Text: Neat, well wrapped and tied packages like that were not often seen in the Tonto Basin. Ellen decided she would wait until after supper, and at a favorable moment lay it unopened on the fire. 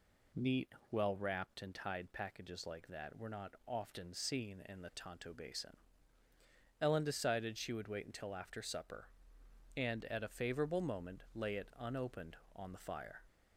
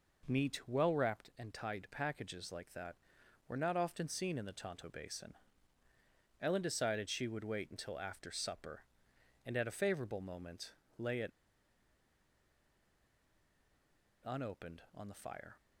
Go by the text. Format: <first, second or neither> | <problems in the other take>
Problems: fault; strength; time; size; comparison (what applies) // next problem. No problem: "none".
first | pauses between "moment" and "lay"; slight; at 10.7 s; 0.26 s long // pauses between "it" and "unopened"; strong; at 11.2 s; 2.9 s long